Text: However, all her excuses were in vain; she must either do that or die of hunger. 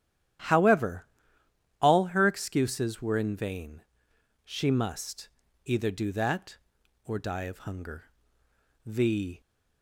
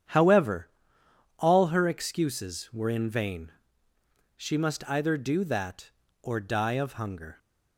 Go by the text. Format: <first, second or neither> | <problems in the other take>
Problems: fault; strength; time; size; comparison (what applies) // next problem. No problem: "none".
second | starts louder than the rest; strong; until 2.2 s; 11 dB; strong in the second // pauses between "must" and "either"; at 5.2 s; 0.38 s long // goes on to say "The"; from 8.8 s on; 0.54 s long